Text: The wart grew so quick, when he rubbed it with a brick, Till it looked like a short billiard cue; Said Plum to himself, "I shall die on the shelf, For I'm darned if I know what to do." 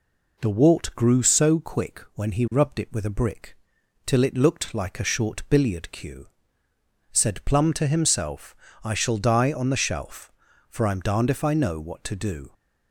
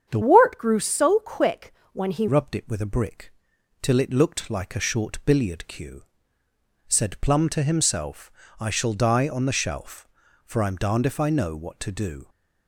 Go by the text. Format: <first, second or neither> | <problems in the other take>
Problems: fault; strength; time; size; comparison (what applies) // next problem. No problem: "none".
first | starts louder than the rest; strong; until 1.1 s; 8 dB // changes voice from "wart" to "he"; from 0.2 to 2.2 s; 2.0 s long